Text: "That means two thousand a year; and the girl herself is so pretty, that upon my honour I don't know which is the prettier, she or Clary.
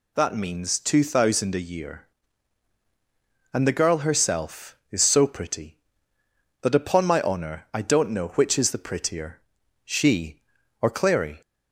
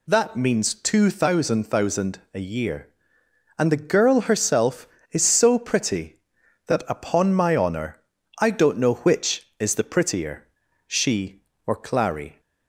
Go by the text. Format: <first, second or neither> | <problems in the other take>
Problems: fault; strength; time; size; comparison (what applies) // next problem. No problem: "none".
first | says "thousand" twice; at 1.6 s // pauses between "honour" and "I"; at 8.0 s; 0.38 s long